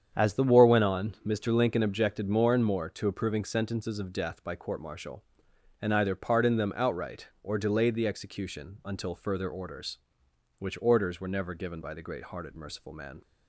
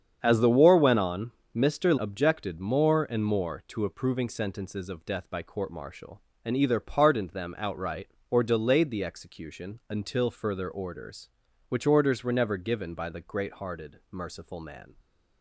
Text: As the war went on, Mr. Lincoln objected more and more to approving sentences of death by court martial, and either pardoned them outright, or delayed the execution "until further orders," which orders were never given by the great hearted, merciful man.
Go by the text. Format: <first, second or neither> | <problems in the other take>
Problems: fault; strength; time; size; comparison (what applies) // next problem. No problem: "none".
first | starts louder than the rest; strong; until 1.2 s; 7.5 dB; strong in the first // skips "Lincoln"; at 1.9 s